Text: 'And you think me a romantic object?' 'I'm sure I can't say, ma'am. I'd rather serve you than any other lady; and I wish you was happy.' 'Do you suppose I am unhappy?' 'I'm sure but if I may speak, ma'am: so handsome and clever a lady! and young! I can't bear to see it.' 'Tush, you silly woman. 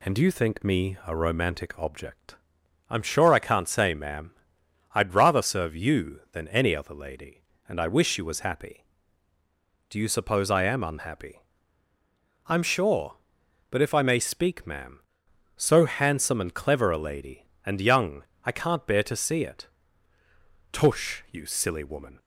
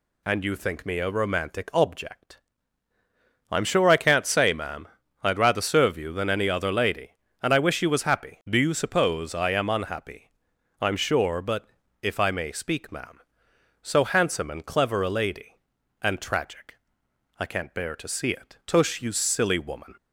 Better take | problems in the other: first | pauses between "but" and "if"; slight; at 11.6 s; 0.34 s long // says "tragic" for "young"; at 16.2 s

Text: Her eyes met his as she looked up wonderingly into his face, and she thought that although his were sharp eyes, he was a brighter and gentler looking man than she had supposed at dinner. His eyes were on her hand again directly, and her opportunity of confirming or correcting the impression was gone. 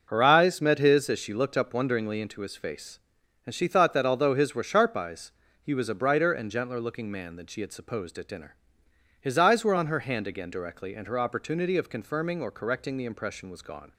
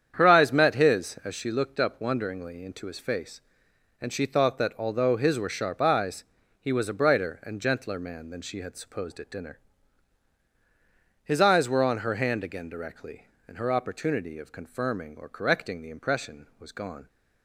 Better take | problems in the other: first | starts louder than the rest; strong; until 1.1 s; 8.5 dB // skips "looking"; at 7.9 s

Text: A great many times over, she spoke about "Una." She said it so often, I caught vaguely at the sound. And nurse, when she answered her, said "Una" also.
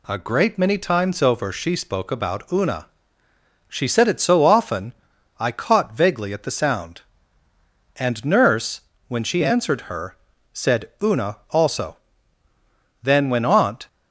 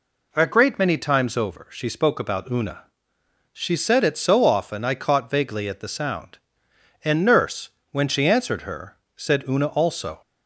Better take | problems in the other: second | goes on to say "Then when Aunt"; noticeable; from 13.0 s on; 0.86 s long

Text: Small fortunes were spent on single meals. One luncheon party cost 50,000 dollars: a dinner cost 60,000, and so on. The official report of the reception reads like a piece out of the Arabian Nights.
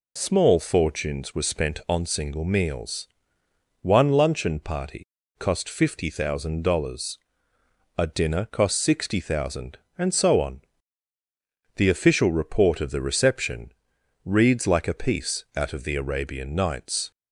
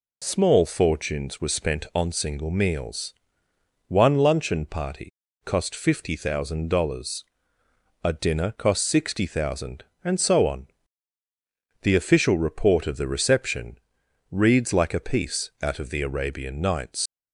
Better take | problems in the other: first | pauses between "party" and "cost"; slight; at 5.1 s; 0.34 s long; slight in the first // pauses between "reception" and "reads"; noticeable; at 13.7 s; 0.52 s long; noticeable in the first // leaves "Nights" unfinished; at 17.0 s; 110 ms

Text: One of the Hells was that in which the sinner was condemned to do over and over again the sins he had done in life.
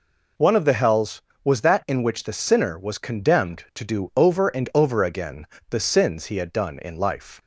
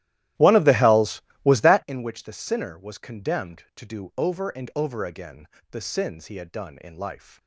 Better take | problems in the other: first | starts louder than the rest; strong; until 1.9 s; 14 dB // pauses between "again" and "the"; slight; at 5.4 s; 0.24 s long; slight in the first

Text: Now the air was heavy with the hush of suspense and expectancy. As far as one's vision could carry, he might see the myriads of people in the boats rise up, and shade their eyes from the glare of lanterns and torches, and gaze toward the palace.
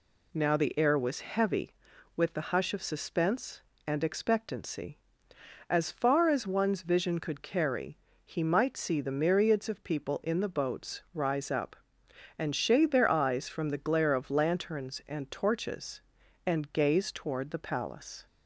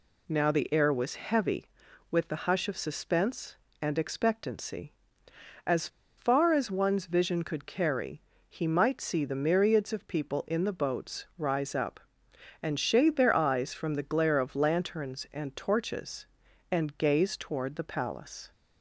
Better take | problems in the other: first | pauses between "As" and "far"; slight; at 5.8 s; 0.30 s long

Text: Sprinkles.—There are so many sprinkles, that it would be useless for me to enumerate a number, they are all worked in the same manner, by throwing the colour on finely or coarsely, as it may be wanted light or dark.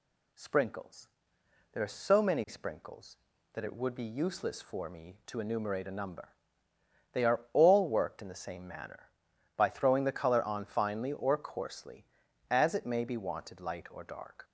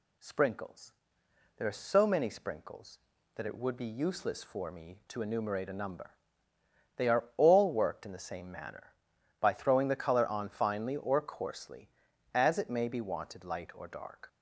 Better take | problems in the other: neither | none

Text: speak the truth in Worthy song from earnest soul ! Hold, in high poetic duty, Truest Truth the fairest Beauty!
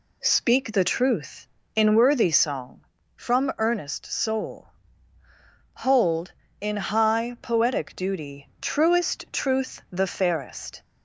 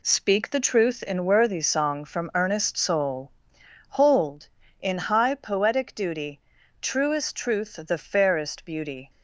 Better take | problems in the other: second | stops before "Beauty"; at 10.8 s

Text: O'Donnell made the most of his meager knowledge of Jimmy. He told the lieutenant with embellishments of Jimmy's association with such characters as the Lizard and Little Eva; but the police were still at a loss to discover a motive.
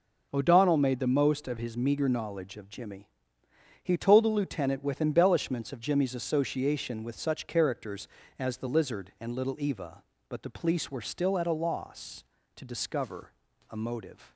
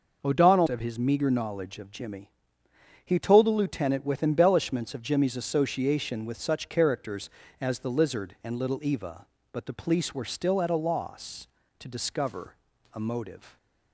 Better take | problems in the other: first | skips "made the most"; at 0.6 s // pauses between "discover" and "a"; at 12.5 s; 0.38 s long; also in the first

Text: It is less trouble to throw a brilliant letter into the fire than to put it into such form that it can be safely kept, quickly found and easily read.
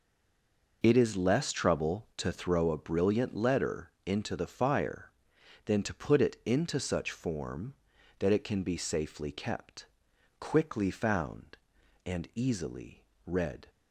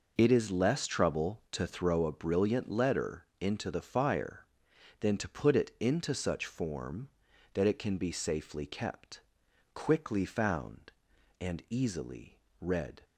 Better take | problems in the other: second | stays silent before the first word; slight; until 0.8 s; 0.8 s long // pauses between "easily" and "read"; slight; at 13.0 s; 0.24 s long; slight in the second

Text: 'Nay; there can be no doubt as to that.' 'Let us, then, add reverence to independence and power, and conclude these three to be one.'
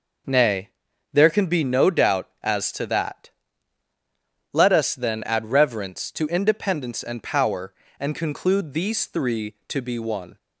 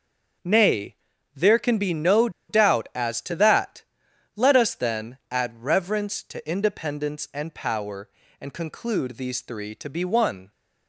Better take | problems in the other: first | starts louder than the rest; strong; until 1.8 s; 7 dB // pauses between "no" and "doubt"; slight; at 2.2 s; 0.19 s long

